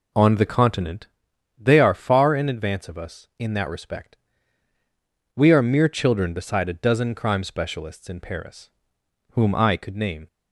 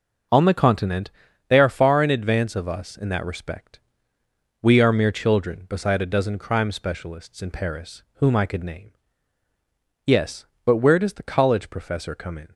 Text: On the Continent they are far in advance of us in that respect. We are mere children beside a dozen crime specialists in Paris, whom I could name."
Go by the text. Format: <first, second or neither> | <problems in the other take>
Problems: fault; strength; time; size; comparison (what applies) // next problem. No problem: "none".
first | pauses between "Continent" and "they"; at 1.0 s; 0.40 s long; noticeable in the first // goes on to say "Yes but where does the college professor come in"; strong; from 10.0 s on; 2.4 s long